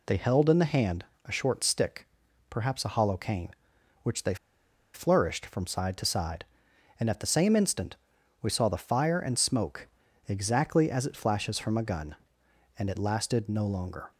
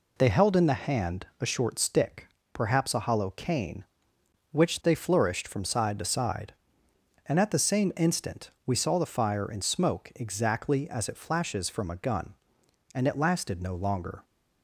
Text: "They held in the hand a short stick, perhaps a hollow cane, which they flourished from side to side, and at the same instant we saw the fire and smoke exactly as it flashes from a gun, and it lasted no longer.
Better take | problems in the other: second | pauses between "hand" and "a"; slight; at 1.0 s; 0.20 s long // pauses between "they" and "flourished"; noticeable; at 4.3 s; 0.59 s long // pauses between "instant" and "we"; noticeable; at 7.9 s; 0.46 s long; slight in the second // pauses between "smoke" and "exactly"; at 9.8 s; 0.40 s long

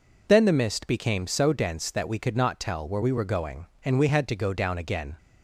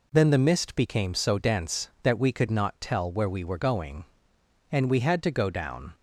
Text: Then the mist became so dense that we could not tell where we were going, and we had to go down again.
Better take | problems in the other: first | stops before "again"; at 5.9 s

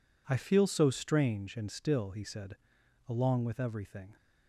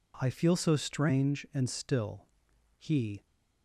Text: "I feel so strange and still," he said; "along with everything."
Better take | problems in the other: first | stops before "said along with everything"; at 3.2 s

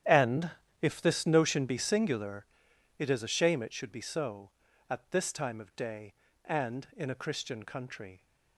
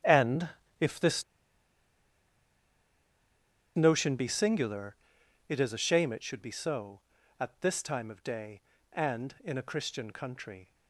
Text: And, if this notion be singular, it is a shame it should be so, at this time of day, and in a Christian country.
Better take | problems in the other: first | starts louder than the rest; strong; until 3.8 s; 10.5 dB; strong in the first // pauses between "this" and "notion"; strong; at 1.2 s; 2.5 s long

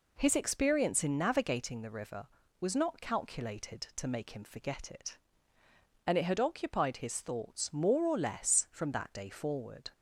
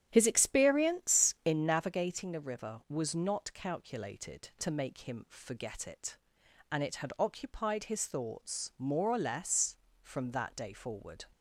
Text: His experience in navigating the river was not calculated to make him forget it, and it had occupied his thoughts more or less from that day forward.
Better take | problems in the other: first | starts louder than the rest; strong; until 1.6 s; 9.5 dB

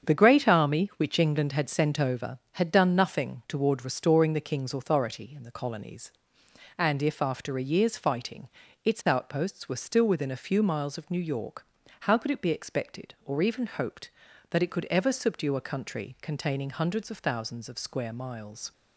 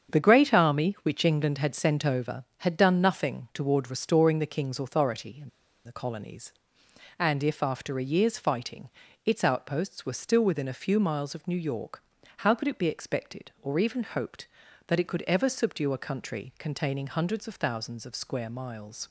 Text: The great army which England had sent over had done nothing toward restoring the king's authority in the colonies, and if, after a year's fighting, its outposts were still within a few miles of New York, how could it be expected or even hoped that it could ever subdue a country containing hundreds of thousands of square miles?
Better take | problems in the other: first | starts louder than the rest; strong; until 1.2 s; 7.5 dB; strong in the first // pauses between "in" and "the"; slight; at 5.4 s; 0.35 s long

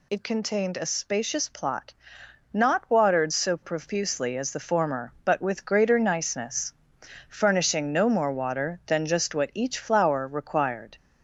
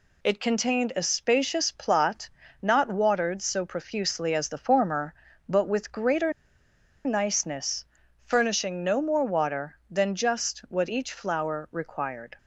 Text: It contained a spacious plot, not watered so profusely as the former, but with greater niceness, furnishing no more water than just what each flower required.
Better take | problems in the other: first | pauses between "greater" and "niceness"; noticeable; at 6.3 s; 0.74 s long

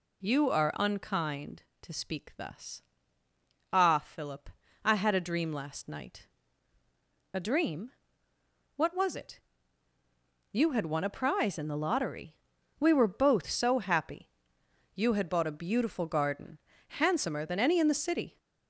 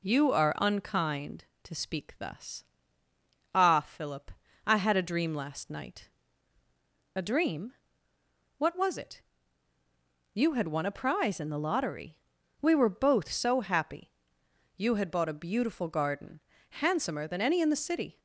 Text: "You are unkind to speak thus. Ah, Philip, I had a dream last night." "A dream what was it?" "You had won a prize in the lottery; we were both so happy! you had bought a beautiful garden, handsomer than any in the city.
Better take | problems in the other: second | gets louder; throughout; 3.5 dB // pauses between "dream" and "what"; noticeable; at 7.8 s; 0.86 s long; noticeable in the second

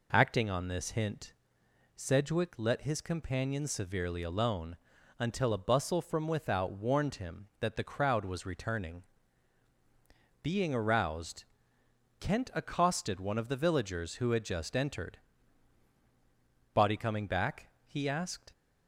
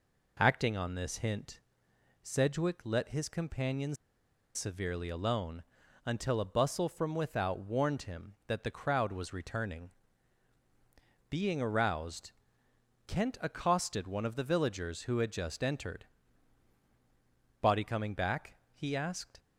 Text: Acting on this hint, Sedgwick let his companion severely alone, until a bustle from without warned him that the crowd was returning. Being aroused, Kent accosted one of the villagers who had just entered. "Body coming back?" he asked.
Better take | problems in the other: first | pauses between "companion" and "severely"; noticeable; at 3.9 s; 0.59 s long

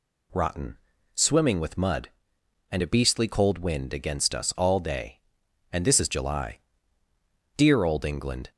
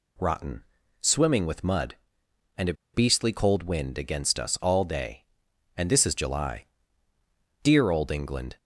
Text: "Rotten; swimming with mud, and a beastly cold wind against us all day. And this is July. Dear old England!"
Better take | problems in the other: first | pauses between "a" and "beastly"; slight; at 2.7 s; 0.20 s long

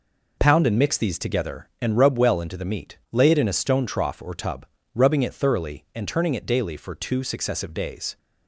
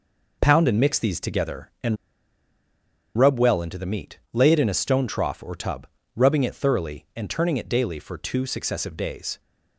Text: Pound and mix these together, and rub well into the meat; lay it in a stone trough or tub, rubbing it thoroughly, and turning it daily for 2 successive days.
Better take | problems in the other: first | pauses between "and" and "rub"; at 1.9 s; 1.2 s long

